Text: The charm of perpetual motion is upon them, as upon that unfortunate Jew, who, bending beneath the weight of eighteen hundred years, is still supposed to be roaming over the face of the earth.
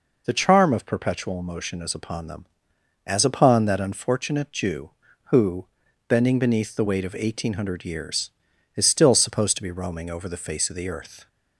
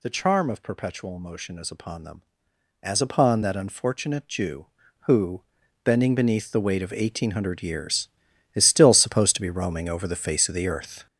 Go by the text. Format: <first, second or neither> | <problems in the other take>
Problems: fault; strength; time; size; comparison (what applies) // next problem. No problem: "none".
first | gets louder; strong; throughout; 7.5 dB